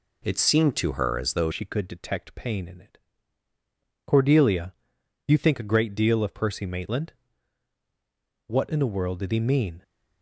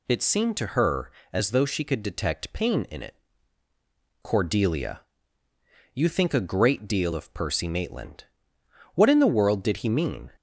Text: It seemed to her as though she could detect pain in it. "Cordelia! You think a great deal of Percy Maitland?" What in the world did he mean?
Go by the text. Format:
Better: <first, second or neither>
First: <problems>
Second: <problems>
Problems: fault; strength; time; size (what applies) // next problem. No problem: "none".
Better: second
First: changes voice at "she"; from 1.5 s on; 8.3 s long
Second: none